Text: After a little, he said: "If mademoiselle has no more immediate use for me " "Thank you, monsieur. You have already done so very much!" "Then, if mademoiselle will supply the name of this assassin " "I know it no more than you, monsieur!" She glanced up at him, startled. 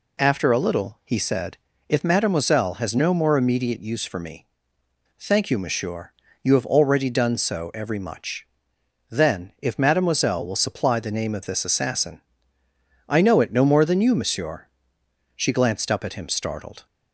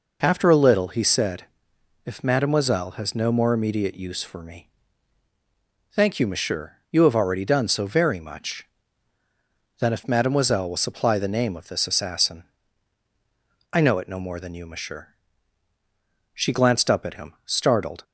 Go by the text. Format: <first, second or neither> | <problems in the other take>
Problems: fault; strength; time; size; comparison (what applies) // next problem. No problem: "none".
second | says "every" for "very"; at 7.7 s